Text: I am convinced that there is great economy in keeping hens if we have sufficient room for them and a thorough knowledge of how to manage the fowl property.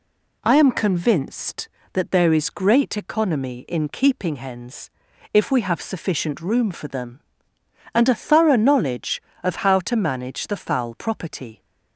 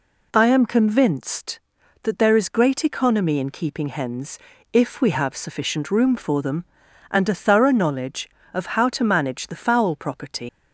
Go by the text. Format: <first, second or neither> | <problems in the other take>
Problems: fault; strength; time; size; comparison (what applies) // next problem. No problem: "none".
first | pauses between "hens" and "if"; slight; at 4.3 s; 0.34 s long; also in the first // leaves "property" unfinished; at 10.4 s; 110 ms